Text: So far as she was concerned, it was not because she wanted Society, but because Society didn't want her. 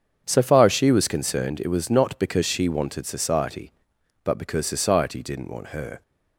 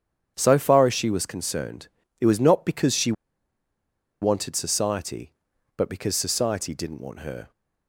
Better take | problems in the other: first | starts louder than the rest; strong; until 1.3 s; 8.5 dB; strong in the first // pauses between "she" and "wanted"; at 3.1 s; 1.0 s long

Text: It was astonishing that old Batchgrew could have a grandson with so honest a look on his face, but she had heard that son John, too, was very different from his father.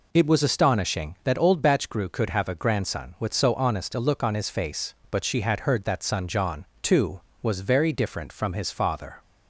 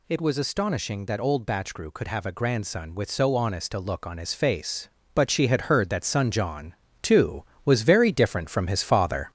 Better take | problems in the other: first | gets louder; noticeable; throughout; 4 dB

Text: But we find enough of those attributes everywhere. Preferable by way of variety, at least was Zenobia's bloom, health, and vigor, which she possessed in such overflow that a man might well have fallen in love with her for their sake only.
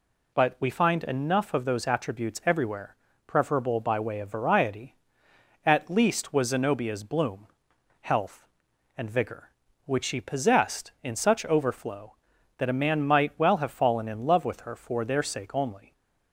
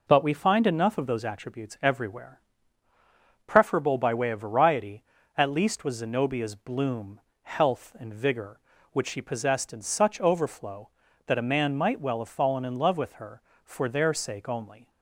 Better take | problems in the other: neither | none

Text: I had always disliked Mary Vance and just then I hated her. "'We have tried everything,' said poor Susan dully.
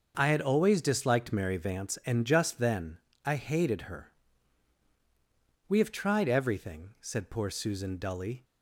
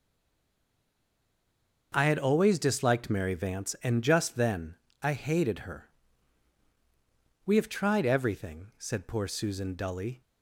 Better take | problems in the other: first | stays silent before the first word; noticeable; until 1.9 s; 1.9 s long // starts louder than the rest; until 2.9 s; 6.5 dB; also in the first // pauses between "then" and "I"; slight; at 4.7 s; 0.28 s long; slight in the first

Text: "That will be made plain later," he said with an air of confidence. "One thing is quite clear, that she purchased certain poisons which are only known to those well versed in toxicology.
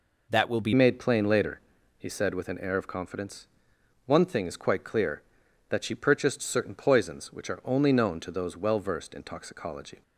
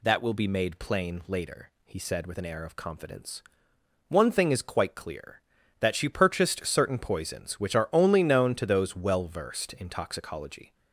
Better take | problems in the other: second | changes voice at "made"; from 0.7 s on; 9.3 s long

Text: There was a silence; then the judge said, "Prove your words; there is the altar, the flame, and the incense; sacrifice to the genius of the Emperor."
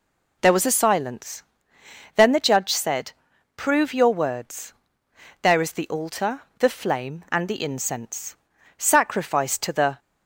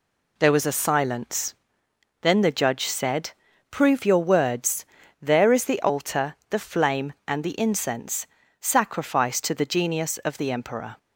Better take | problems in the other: second | stops before "genius of the Emperor"; at 9.9 s

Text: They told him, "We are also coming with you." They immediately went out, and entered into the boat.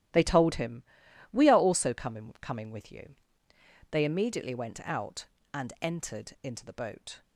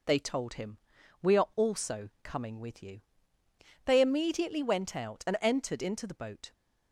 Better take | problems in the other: second | starts louder than the rest; strong; until 1.6 s; 13.5 dB // says "coming" twice; at 2.4 s

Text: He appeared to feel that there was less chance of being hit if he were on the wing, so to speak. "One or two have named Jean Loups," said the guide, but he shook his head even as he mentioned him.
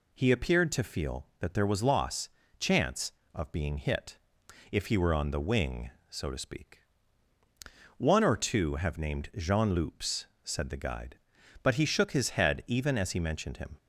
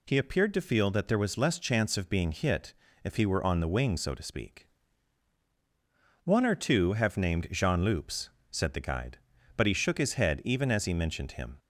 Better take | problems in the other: second | says "loss" for "less"; at 1.8 s // pauses between "hit" and "if"; noticeable; at 4.1 s; 0.52 s long; slight in the second

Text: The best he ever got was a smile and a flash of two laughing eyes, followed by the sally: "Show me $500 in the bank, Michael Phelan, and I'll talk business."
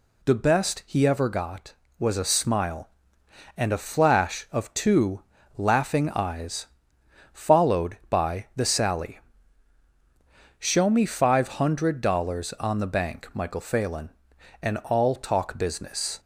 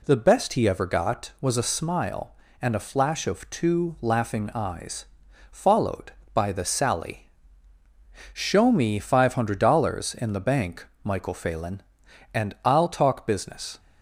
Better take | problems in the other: second | pauses between "two" and "laughing"; slight; at 5.2 s; 0.36 s long // says "on" for "in"; at 12.5 s

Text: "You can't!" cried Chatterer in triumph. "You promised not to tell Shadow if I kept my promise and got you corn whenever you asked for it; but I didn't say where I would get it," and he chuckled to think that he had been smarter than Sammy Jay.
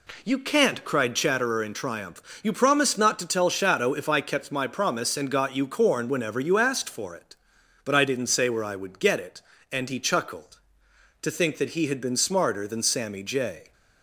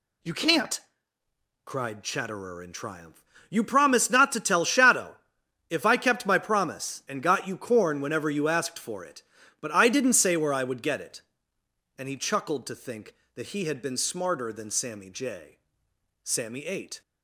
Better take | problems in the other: first | pauses between "Shadow" and "if"; noticeable; at 5.1 s; 0.56 s long // goes on to say "Sammy ate"; noticeable; from 16.2 s on; 0.78 s long

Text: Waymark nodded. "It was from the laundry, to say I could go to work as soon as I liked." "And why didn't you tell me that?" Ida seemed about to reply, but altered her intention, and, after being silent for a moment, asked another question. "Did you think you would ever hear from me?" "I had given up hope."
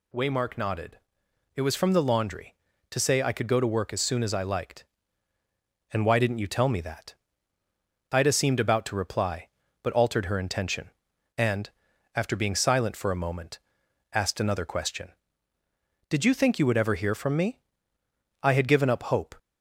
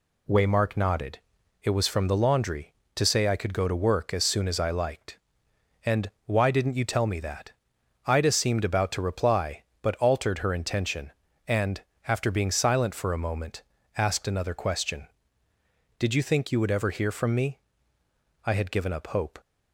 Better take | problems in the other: neither | none

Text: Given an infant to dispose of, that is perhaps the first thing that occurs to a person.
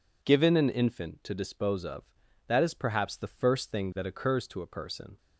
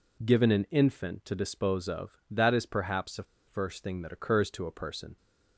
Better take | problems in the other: first | pauses between "the" and "first"; slight; at 3.2 s; 0.23 s long

